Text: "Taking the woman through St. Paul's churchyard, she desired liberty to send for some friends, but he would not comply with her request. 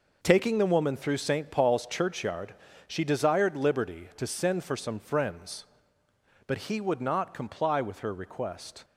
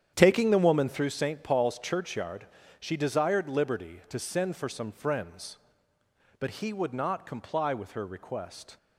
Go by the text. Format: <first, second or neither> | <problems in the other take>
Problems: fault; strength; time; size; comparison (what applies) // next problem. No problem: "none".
first | starts louder than the rest; strong; until 1.1 s; 9 dB